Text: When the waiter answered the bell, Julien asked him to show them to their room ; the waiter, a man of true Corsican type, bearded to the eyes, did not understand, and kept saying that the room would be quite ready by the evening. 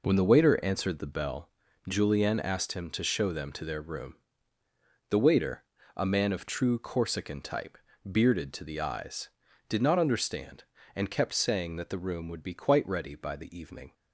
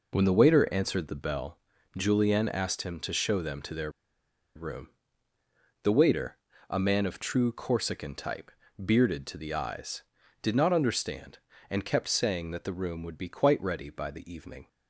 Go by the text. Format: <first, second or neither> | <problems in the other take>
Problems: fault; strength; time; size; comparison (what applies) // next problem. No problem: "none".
first | pauses between "their" and "room"; noticeable; at 3.8 s; 0.65 s long